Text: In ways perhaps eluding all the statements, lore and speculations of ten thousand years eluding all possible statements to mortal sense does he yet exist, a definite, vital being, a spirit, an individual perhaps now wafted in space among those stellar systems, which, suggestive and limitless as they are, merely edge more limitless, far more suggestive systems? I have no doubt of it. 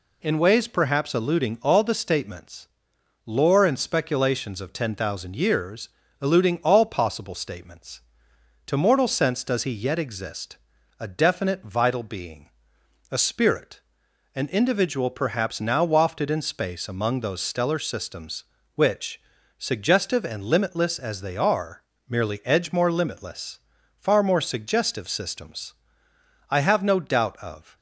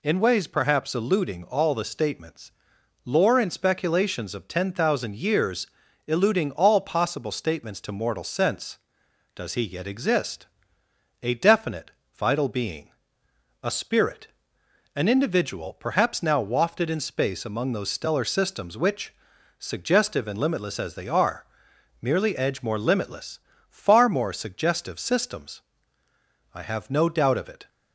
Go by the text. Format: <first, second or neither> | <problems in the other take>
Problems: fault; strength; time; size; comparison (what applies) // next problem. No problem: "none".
second | pauses between "years" and "eluding"; slight; at 5.8 s; 0.32 s long; also in the second // stops before "it"; at 27.7 s